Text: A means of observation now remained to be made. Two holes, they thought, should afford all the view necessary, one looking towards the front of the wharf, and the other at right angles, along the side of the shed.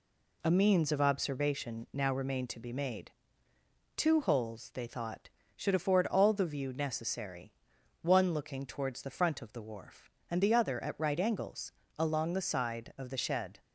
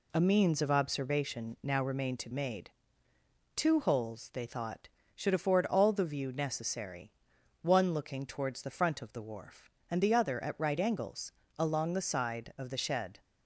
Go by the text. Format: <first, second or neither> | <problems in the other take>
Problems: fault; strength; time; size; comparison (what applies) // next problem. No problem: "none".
first | skips "be"; at 2.3 s